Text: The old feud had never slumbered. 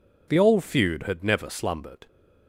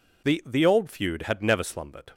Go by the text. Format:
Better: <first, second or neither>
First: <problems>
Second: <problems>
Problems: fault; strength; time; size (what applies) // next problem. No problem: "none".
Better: first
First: none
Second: says "The" twice; at 0.4 s